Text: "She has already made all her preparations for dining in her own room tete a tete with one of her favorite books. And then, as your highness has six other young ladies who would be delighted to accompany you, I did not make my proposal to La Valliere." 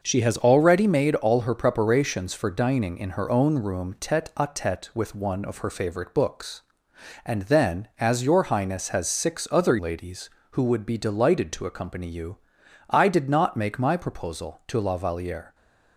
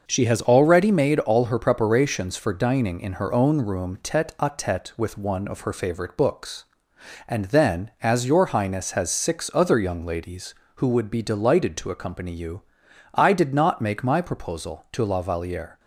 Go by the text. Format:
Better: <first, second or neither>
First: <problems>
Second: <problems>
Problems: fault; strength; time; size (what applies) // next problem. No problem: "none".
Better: second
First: skips "young"; at 9.7 s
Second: none